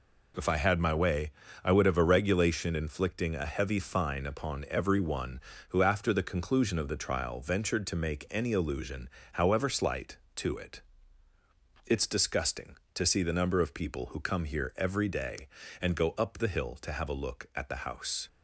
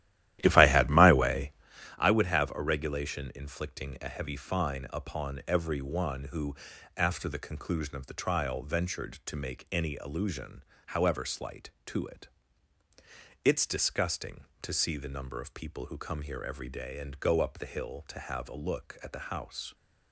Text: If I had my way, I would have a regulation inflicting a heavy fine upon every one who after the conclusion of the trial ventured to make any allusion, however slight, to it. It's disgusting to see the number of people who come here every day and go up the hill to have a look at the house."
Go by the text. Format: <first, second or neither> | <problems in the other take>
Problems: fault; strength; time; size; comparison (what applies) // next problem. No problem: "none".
first | starts louder than the rest; strong; until 1.9 s; 13.5 dB // pauses between "who" and "after"; at 6.5 s; 0.40 s long